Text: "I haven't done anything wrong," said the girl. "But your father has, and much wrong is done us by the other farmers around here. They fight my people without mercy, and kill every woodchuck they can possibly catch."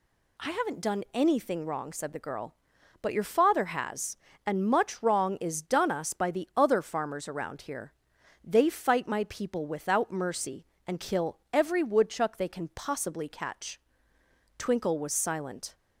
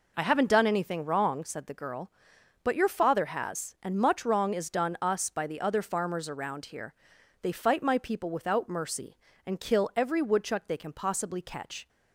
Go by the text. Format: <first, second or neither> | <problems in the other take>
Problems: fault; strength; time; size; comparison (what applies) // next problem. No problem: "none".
second | pauses between "kill" and "every"; slight; at 11.3 s; 0.16 s long // goes on to say "Twinkle was silent"; noticeable; from 14.5 s on; 1.1 s long